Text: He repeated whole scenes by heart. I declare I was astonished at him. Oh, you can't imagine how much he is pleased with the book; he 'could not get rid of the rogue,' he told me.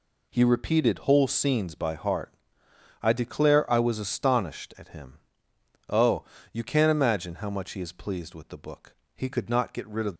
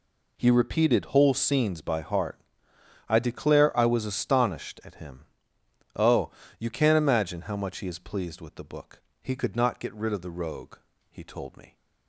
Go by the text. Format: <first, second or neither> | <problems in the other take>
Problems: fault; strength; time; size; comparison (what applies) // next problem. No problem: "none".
second | stops before "the rogue he told me"; at 10.1 s